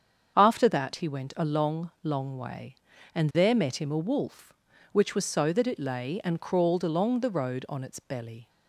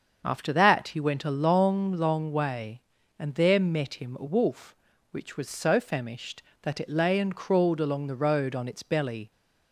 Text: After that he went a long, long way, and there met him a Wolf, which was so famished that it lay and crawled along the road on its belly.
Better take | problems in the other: second | starts louder than the rest; strong; until 1.3 s; 7.5 dB; also in the second // skips "famished"; at 5.5 s

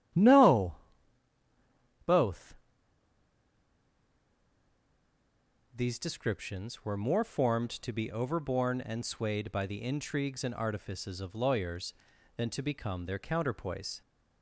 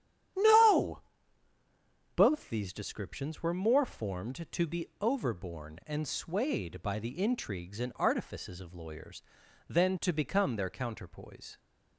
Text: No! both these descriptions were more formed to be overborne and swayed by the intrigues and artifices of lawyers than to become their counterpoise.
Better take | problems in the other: second | starts louder than the rest; strong; until 2.4 s; 12 dB; strong in the second // pauses between "both" and "these"; strong; at 2.5 s; 3.1 s long

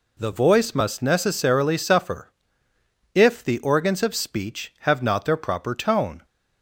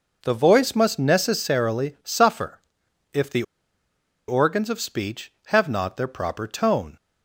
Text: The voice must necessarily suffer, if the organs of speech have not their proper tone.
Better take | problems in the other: first | pauses between "the" and "organs"; noticeable; at 3.4 s; 0.85 s long

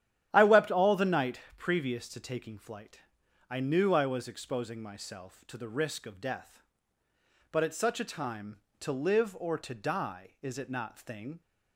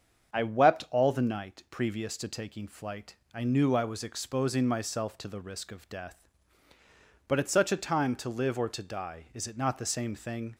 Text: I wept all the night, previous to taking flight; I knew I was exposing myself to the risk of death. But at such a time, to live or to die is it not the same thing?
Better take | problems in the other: second | starts louder than the rest; strong; until 1.3 s; 11 dB; also in the second // skips "the same"; at 10.9 s

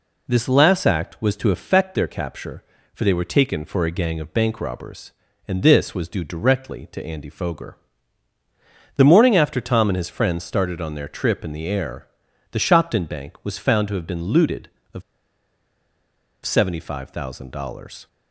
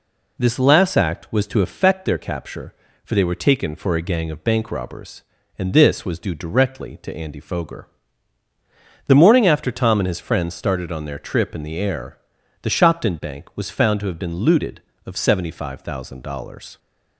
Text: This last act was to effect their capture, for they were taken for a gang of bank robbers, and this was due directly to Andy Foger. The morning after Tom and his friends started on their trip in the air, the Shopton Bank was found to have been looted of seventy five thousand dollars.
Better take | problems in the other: second | pauses between "of" and "seventy"; strong; at 15.0 s; 1.4 s long

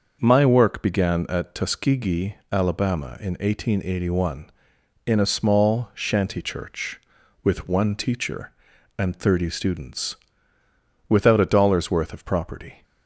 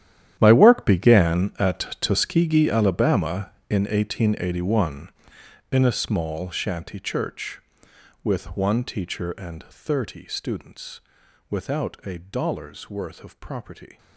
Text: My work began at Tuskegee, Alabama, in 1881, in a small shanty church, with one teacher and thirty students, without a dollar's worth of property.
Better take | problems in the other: first | gets quieter; strong; throughout; 17 dB // starts louder than the rest; strong; until 1.4 s; 11 dB; also in the first

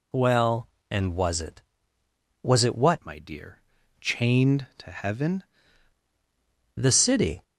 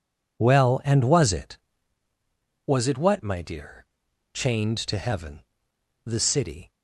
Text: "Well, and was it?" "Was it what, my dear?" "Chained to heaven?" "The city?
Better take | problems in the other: second | changes voice from "my" to "heaven"; from 3.0 to 5.4 s; 2.4 s long

